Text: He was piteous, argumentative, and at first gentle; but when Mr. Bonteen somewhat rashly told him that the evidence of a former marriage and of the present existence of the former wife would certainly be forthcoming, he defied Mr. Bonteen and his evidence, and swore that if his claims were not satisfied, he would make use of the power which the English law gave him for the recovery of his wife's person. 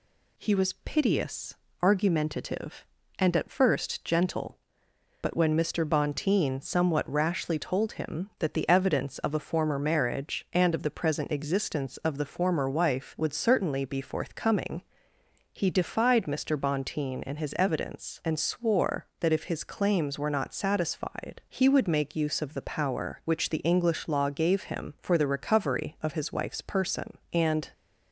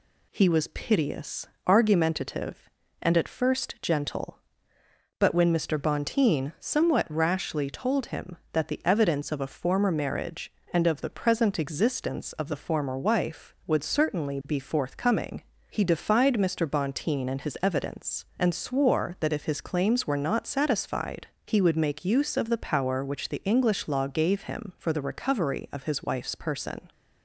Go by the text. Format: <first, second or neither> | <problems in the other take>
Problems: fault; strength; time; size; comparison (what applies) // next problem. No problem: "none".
second | goes on to say "And"; slight; from 27.3 s on; 0.38 s long